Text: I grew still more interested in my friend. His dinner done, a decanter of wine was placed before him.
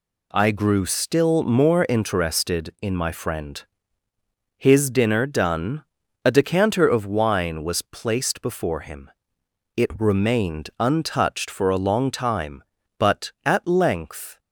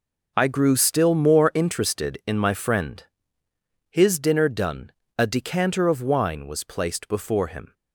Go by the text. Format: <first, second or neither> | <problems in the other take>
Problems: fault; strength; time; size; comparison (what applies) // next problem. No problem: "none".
second | goes on to say "It remained untouched for a long time but at length"; strong; from 9.7 s on; 4.6 s long